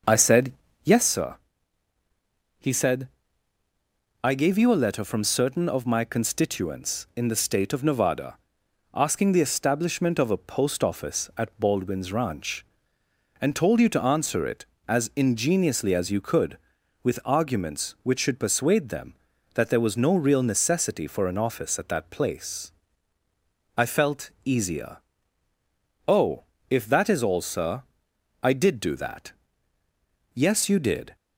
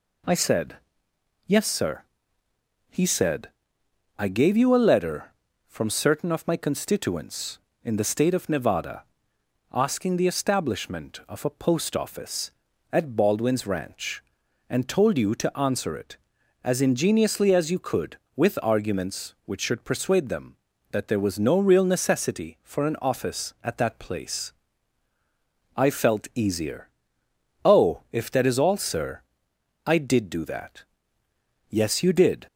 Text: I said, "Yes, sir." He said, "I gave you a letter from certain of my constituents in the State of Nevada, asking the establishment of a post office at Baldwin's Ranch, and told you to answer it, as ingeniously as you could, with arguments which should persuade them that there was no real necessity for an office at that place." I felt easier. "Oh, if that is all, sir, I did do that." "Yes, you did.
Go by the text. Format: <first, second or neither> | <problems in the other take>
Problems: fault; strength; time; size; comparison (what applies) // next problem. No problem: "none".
second | starts louder than the rest; until 1.1 s; 6.5 dB